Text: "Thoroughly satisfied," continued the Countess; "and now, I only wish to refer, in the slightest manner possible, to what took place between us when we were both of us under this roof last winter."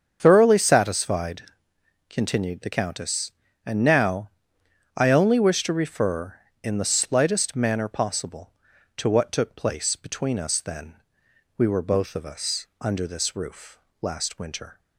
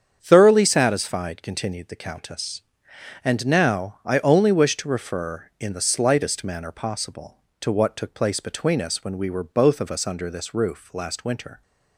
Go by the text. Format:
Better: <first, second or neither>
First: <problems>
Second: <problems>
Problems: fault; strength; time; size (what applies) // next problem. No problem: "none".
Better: second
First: starts louder than the rest; until 1.2 s; 7 dB // says "then" for "when"; at 10.6 s // pauses between "roof" and "last"; slight; at 13.7 s; 0.24 s long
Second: starts louder than the rest; strong; until 1.2 s; 7.5 dB